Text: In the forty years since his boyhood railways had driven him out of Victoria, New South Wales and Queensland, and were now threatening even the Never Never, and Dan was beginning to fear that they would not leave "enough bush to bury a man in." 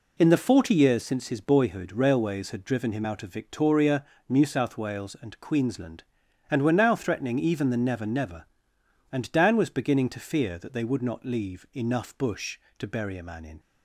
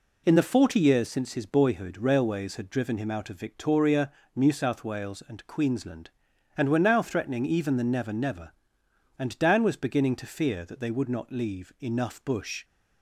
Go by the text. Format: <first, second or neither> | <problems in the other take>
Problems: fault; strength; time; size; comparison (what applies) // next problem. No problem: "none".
first | stops before "to bury a man in"; at 12.6 s